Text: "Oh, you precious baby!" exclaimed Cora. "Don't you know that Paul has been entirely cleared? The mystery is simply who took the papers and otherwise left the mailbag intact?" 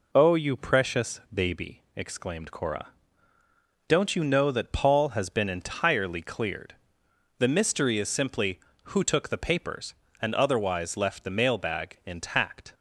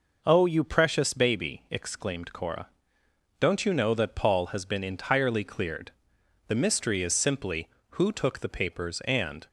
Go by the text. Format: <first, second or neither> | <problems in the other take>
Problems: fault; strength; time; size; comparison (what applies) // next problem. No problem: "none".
first | stops before "otherwise left the mailbag intact"; at 9.4 s